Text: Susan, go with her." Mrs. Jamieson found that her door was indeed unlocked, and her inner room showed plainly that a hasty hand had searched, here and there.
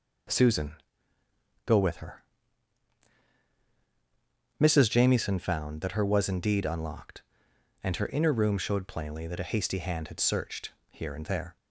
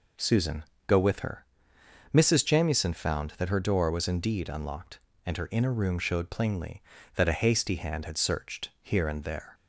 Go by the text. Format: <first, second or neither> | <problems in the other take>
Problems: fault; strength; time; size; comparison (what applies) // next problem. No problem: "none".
second | skips "door"; at 6.0 s